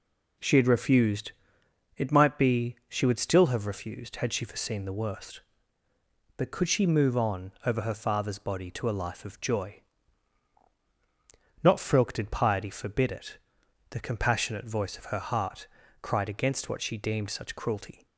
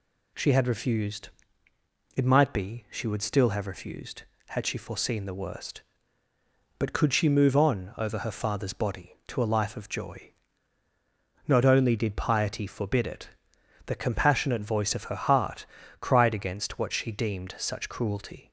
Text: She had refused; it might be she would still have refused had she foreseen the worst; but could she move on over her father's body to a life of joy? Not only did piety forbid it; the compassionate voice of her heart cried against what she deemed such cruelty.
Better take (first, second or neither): second